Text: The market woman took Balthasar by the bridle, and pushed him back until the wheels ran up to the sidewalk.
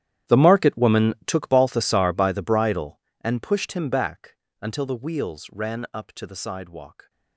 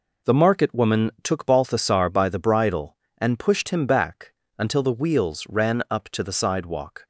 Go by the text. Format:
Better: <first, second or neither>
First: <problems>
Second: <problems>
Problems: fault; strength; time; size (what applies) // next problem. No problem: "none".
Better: second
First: gets quieter; strong; throughout; 20 dB // pauses between "back" and "until"; slight; at 4.3 s; 0.26 s long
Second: pauses between "back" and "until"; slight; at 4.3 s; 0.26 s long